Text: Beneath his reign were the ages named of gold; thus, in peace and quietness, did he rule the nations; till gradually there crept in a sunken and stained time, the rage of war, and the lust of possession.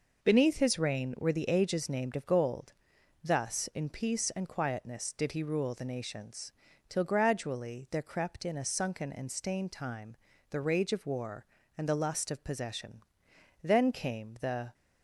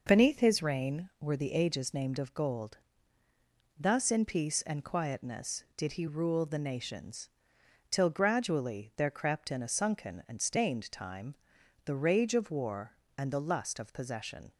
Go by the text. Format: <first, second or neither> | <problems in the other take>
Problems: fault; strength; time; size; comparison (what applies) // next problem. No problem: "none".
second | goes on to say "Then came the"; noticeable; from 13.6 s on; 1.1 s long